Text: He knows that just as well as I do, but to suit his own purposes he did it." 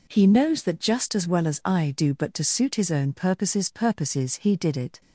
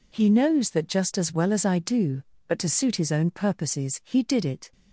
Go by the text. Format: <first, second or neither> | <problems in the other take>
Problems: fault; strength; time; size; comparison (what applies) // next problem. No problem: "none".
second | says "purposes" twice; at 3.7 s